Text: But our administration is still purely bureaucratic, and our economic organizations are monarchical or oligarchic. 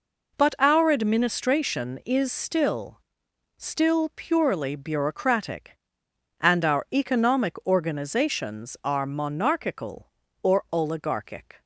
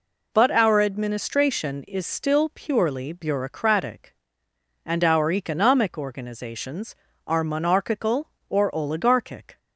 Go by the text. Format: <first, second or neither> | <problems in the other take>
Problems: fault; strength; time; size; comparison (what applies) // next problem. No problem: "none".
second | says "still" twice; at 3.5 s